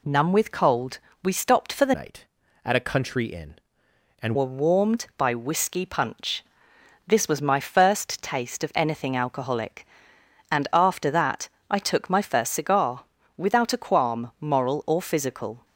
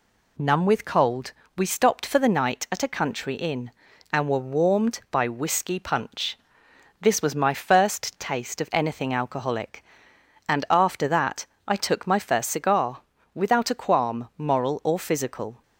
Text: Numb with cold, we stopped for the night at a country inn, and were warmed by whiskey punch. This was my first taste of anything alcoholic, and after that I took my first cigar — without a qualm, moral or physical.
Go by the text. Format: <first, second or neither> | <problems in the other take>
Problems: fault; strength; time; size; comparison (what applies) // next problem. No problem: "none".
second | changes voice from "night" to "and"; from 1.9 to 4.3 s; 2.4 s long // pauses between "that" and "I"; slight; at 11.4 s; 0.24 s long; slight in the second